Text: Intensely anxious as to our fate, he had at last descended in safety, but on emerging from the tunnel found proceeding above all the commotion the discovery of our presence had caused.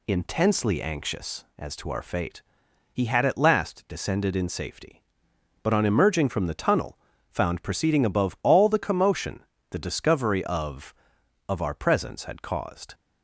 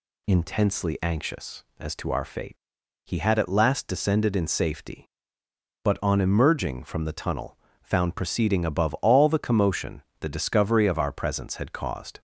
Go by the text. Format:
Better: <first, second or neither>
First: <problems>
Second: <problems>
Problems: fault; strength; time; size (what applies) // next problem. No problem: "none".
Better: second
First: pauses between "tunnel" and "found"; slight; at 6.9 s; 0.32 s long // pauses between "commotion" and "the"; slight; at 9.3 s; 0.30 s long // says "of" twice; at 11.4 s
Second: pauses between "tunnel" and "found"; slight; at 7.5 s; 0.24 s long // pauses between "commotion" and "the"; slight; at 10.0 s; 0.18 s long